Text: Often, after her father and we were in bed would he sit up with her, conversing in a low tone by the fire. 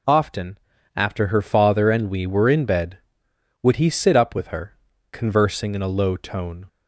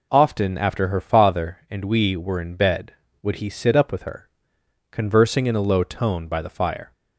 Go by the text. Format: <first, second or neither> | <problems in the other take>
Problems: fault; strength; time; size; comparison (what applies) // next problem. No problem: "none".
second | stops before "by the fire"; at 6.6 s